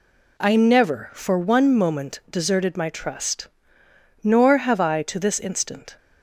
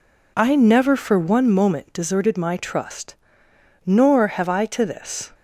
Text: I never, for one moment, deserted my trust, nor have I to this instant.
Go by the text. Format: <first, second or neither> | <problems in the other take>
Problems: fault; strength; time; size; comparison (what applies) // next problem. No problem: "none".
first | stops before "instant"; at 5.3 s